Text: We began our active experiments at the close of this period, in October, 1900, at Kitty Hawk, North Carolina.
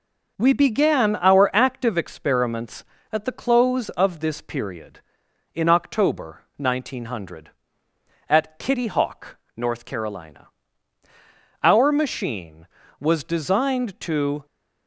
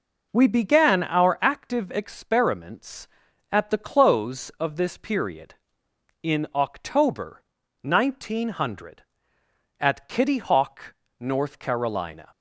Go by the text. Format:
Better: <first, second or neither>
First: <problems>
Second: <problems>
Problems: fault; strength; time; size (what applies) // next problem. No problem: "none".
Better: second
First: goes on to say "Our machine was designed to"; strong; from 11.6 s on; 2.8 s long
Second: none